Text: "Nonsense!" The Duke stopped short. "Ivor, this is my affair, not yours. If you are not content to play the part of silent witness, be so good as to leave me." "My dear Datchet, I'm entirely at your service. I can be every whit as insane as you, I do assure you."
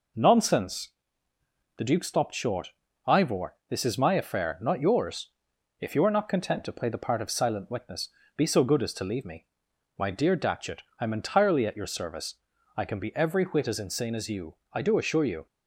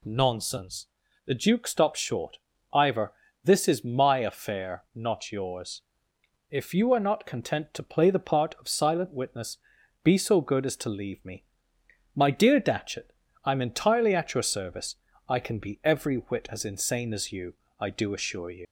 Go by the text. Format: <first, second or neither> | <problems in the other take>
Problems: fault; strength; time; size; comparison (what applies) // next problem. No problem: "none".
first | leaves "you" unfinished; at 18.6 s; 85 ms